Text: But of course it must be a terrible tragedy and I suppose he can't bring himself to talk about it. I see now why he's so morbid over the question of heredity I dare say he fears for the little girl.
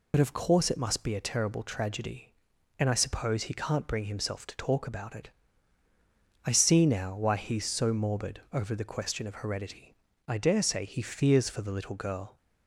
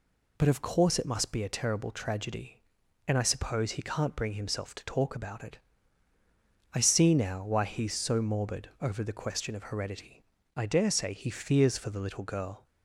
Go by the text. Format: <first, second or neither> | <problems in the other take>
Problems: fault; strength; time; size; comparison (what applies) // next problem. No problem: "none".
second | loses the start of "But"; at 0.1 s; 45 ms // pauses between "heredity" and "I"; slight; at 9.9 s; 0.36 s long; slight in the second